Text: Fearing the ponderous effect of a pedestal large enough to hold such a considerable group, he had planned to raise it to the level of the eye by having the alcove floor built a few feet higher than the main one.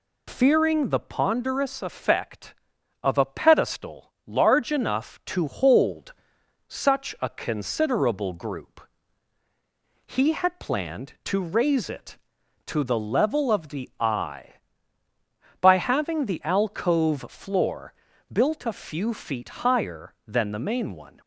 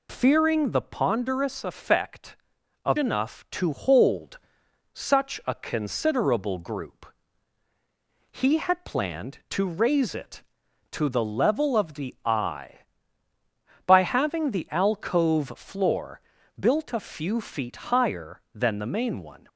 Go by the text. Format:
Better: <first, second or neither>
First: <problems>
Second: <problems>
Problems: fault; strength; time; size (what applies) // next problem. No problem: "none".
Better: first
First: pauses between "hold" and "such"; noticeable; at 6.1 s; 0.56 s long // pauses between "floor" and "built"; slight; at 17.9 s; 0.36 s long // pauses between "feet" and "higher"; slight; at 19.4 s; 0.16 s long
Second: skips "a pedestal large"; at 2.9 s // pauses between "hold" and "such"; noticeable; at 4.3 s; 0.56 s long // pauses between "floor" and "built"; slight; at 16.2 s; 0.36 s long // pauses between "feet" and "higher"; slight; at 17.7 s; 0.16 s long